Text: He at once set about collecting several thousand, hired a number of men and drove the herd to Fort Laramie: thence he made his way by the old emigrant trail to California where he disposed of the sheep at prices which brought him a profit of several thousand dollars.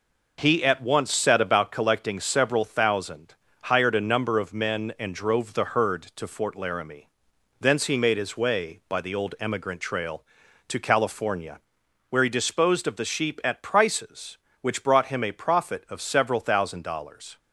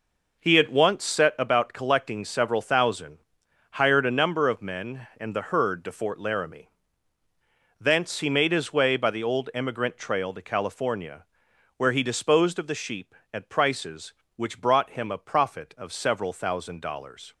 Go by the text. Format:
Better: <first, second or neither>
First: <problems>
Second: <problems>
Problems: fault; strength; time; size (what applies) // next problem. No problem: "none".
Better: first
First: pauses between "California" and "where"; noticeable; at 11.5 s; 0.50 s long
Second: skips "drove"; at 5.3 s // pauses between "California" and "where"; noticeable; at 11.2 s; 0.52 s long